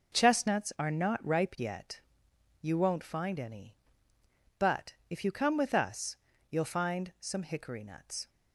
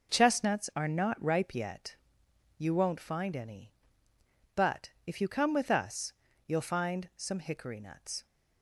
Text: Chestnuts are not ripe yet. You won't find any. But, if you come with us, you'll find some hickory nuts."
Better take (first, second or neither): neither